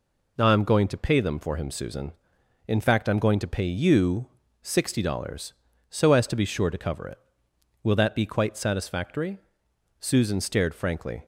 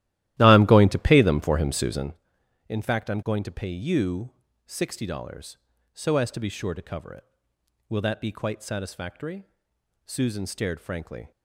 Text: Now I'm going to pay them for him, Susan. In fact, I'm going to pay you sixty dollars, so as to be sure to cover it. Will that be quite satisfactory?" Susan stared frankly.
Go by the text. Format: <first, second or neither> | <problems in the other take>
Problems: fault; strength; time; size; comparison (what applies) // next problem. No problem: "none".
first | starts louder than the rest; strong; until 2.3 s; 14 dB // pauses between "you" and "sixty"; slight; at 4.3 s; 0.34 s long; slight in the first